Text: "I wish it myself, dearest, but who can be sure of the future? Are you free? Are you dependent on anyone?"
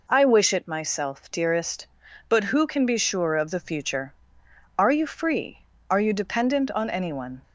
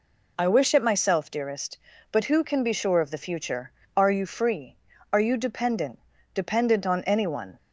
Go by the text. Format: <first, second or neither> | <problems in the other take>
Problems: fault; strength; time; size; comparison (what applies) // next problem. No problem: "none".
first | says "dependent" twice; at 6.3 s